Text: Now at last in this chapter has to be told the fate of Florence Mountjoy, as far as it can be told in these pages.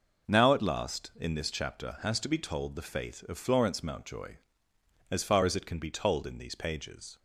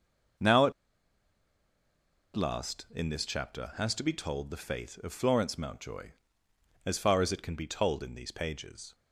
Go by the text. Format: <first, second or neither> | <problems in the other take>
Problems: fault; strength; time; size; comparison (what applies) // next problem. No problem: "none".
first | pauses between "at" and "last"; strong; at 0.7 s; 1.6 s long